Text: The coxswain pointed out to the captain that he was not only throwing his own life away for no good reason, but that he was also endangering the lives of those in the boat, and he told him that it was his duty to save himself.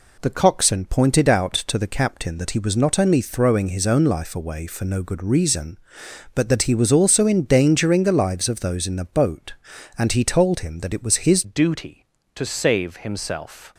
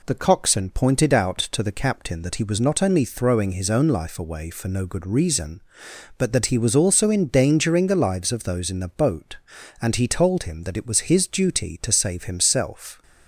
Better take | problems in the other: second | changes voice at "duty"; from 11.4 s on; 2.3 s long

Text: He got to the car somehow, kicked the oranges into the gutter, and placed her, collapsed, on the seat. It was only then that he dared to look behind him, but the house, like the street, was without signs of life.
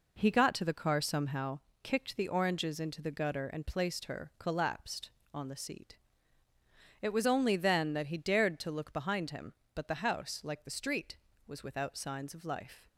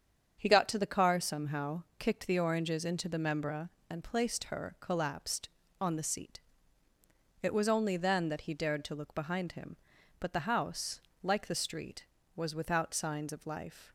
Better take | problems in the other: first | starts louder than the rest; strong; until 1.3 s; 7.5 dB // says "membra" for "gutter"; at 3.1 s

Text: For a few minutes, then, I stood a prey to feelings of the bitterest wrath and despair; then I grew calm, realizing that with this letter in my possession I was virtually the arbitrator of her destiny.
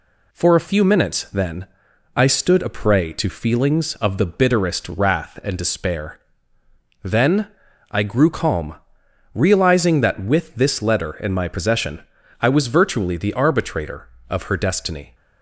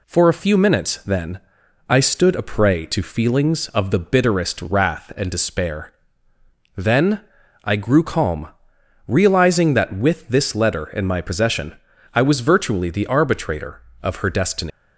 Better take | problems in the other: first | pauses between "then" and "I"; at 7.2 s; 0.42 s long; also in the first // pauses between "possession" and "I"; at 11.7 s; 0.38 s long; also in the first // leaves "destiny" unfinished; at 14.7 s; 175 ms

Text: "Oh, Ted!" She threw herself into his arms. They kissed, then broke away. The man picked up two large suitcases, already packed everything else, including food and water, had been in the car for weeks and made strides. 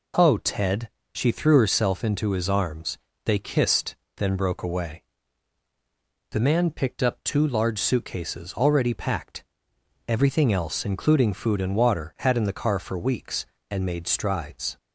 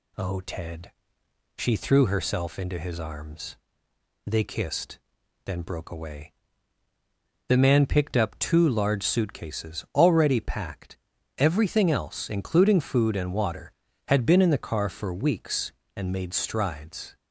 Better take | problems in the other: second | pauses between "packed" and "everything"; noticeable; at 9.4 s; 0.64 s long; also in the second // skips "been"; at 12.3 s

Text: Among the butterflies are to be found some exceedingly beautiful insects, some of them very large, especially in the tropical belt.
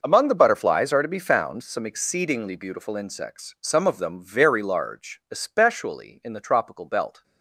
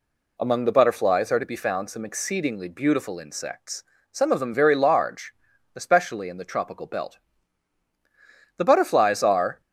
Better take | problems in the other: first | goes on to say "The butterflies are"; noticeable; from 8.5 s on; 1.0 s long

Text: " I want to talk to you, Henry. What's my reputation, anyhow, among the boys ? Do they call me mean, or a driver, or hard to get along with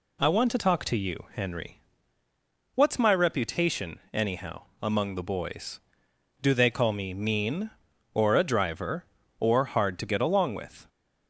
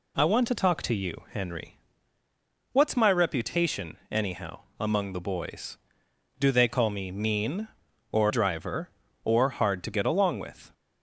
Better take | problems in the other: first | skips "a"; at 8.2 s

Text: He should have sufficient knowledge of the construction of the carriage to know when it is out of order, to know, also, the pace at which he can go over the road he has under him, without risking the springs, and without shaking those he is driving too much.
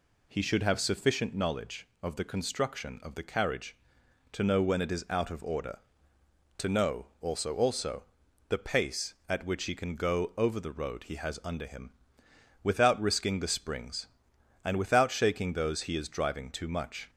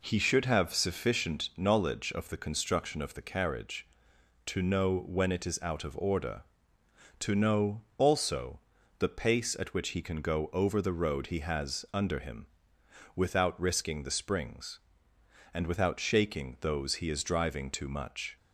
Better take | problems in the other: second | says "also" twice; at 7.5 s

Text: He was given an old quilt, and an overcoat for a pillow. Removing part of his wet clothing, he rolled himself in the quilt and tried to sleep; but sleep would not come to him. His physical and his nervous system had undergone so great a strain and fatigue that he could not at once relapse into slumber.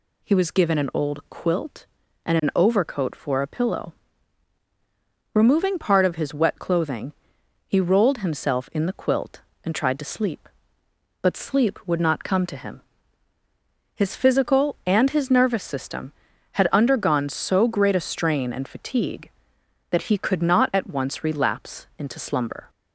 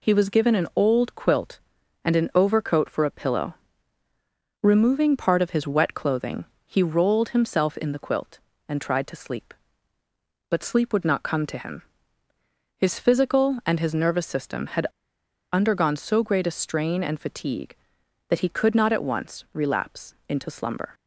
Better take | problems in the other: first | pauses between "had" and "undergone"; noticeable; at 14.9 s; 0.62 s long // pauses between "relapse" and "into"; slight; at 20.1 s; 0.16 s long

